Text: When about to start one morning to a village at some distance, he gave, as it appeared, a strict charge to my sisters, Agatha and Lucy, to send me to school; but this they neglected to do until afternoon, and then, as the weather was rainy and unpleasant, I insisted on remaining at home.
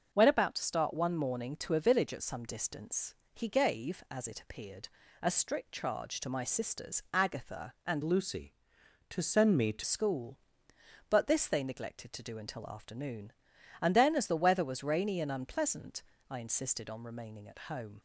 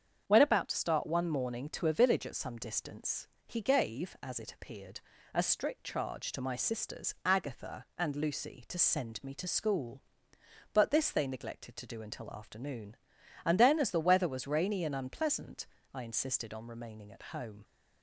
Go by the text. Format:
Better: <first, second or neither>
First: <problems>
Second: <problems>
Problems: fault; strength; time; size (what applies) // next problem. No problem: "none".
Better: second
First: starts louder than the rest; until 1.1 s; 6.5 dB // changes voice from "Lucy" to "to"; from 8.0 to 9.8 s; 1.8 s long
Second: starts louder than the rest; strong; until 1.2 s; 7.5 dB